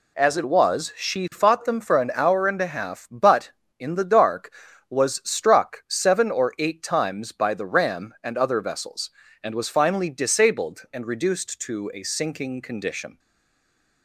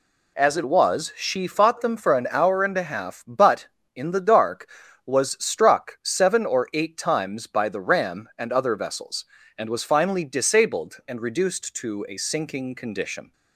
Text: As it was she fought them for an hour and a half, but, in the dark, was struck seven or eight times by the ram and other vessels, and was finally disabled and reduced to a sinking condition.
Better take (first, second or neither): second